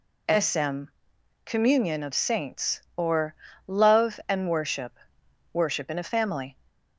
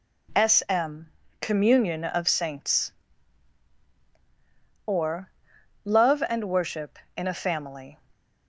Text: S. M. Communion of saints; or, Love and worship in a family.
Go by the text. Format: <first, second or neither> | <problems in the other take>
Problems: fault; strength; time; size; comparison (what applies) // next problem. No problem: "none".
second | pauses between "M" and "Communion"; noticeable; at 0.8 s; 0.58 s long; slight in the second // says "worship" twice; at 5.5 s